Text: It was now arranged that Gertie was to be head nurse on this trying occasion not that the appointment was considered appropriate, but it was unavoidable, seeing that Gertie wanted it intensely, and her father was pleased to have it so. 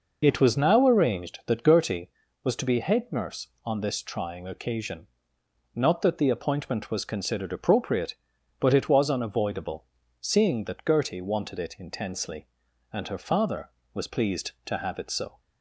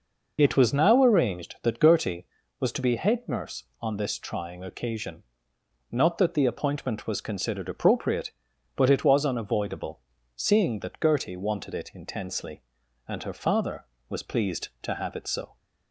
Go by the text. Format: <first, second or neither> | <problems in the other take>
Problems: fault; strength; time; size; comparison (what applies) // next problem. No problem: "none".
neither | pauses between "occasion" and "not"; noticeable; the same in both